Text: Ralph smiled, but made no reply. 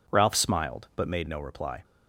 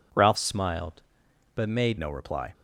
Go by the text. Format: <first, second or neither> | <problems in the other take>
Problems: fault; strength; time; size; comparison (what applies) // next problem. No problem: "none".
first | changes voice from "smiled" to "made"; from 0.3 to 1.9 s; 1.6 s long